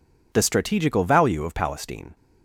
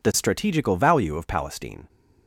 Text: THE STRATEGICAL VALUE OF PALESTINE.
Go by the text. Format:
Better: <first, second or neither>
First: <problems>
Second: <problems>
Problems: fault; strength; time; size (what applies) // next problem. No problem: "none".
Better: neither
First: none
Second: none